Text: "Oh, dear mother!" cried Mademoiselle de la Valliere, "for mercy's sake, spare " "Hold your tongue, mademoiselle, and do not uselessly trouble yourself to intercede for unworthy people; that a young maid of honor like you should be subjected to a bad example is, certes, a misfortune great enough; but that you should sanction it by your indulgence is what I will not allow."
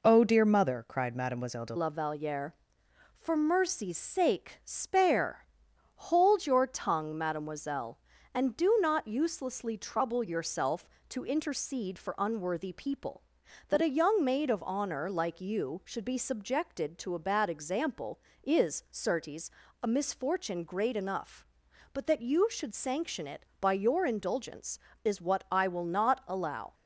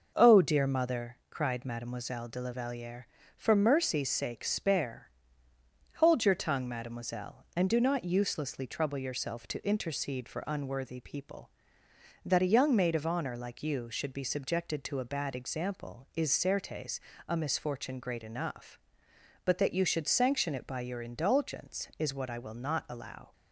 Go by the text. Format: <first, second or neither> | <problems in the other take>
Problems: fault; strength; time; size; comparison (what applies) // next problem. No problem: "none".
second | changes voice at "la"; from 1.7 s on; 25.0 s long